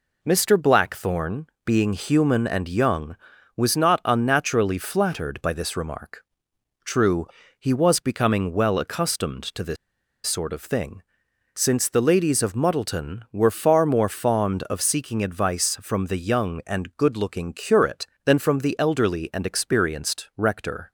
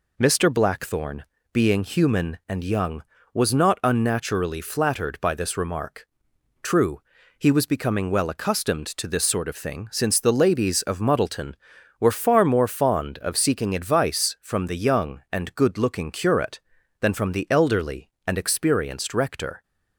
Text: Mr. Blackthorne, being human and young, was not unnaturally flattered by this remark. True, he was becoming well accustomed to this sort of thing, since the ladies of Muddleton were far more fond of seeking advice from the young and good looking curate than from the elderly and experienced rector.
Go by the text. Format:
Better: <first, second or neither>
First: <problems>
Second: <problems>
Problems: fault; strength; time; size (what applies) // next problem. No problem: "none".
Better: second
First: pauses between "this" and "sort"; noticeable; at 9.7 s; 0.50 s long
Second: none